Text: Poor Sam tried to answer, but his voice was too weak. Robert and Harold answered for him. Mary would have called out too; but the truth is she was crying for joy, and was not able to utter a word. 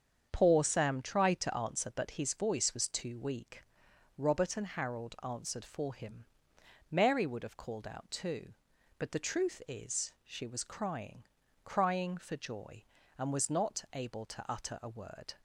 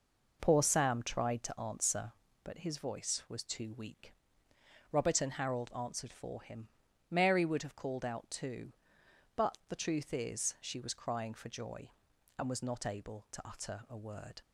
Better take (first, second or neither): second